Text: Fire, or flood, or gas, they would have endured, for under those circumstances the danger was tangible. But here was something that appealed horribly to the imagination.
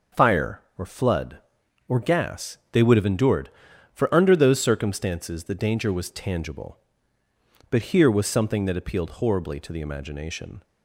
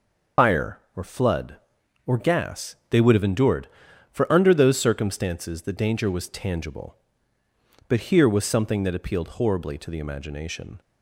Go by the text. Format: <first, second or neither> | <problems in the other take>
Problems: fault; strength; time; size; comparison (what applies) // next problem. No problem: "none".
first | loses the start of "Fire"; at 0.3 s; 60 ms